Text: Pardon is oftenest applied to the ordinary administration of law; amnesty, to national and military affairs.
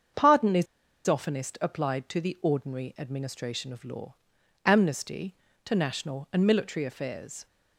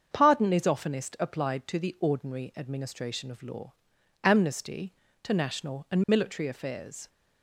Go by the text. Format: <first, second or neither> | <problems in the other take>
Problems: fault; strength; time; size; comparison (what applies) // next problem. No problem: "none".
second | starts louder than the rest; until 1.5 s; 7 dB; also in the second // pauses between "is" and "oftenest"; at 0.6 s; 0.41 s long